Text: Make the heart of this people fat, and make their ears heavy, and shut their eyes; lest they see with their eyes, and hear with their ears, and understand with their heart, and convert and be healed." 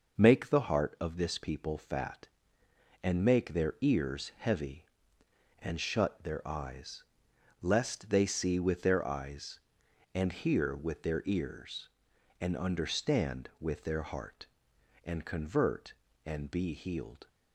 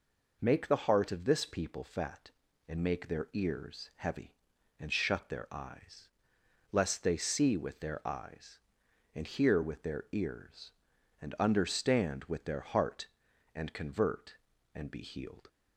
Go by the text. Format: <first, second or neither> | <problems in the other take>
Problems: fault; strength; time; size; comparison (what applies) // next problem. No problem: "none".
neither | none